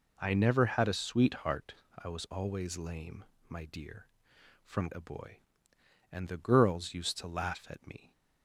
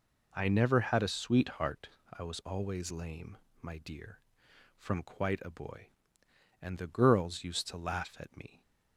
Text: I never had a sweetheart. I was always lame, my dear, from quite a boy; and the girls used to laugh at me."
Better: second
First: skips "quite"; at 4.9 s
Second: none

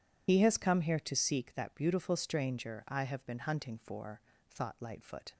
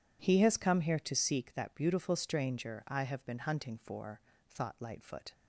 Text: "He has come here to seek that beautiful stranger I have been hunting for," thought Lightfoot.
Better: second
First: loses the start of "He"; at 0.2 s; 85 ms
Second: none

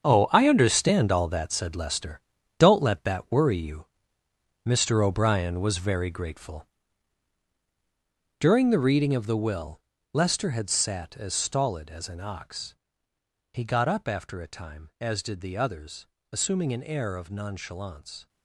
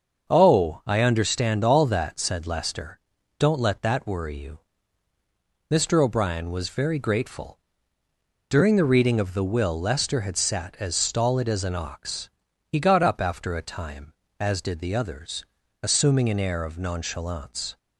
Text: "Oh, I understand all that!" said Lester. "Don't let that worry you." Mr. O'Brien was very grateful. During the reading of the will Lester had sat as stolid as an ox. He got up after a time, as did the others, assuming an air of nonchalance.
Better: second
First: gets quieter; strong; throughout; 11.5 dB // starts louder than the rest; strong; until 1.0 s; 7.5 dB // pauses between "will" and "Lester"; slight; at 9.8 s; 0.32 s long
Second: starts louder than the rest; until 1.3 s; 6.5 dB

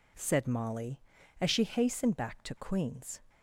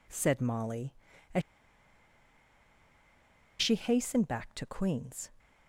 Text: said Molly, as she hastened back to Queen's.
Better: first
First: none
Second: pauses between "as" and "she"; strong; at 1.4 s; 2.2 s long

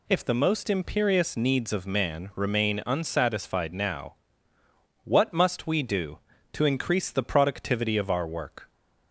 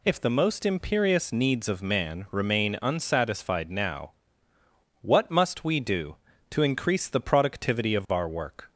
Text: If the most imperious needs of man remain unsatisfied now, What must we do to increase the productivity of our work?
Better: neither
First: none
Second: none

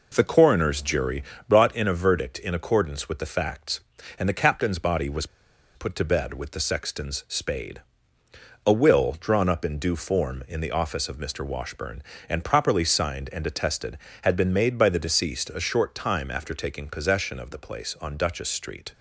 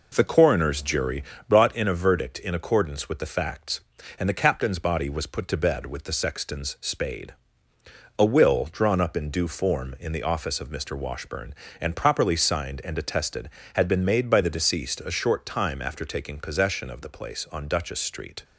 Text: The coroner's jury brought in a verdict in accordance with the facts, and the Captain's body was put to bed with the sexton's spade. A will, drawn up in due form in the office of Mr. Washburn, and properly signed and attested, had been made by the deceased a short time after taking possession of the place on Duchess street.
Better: second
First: pauses between "jury" and "brought"; slight; at 1.2 s; 0.26 s long // pauses between "was" and "put"; noticeable; at 5.2 s; 0.50 s long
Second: pauses between "jury" and "brought"; slight; at 1.2 s; 0.26 s long

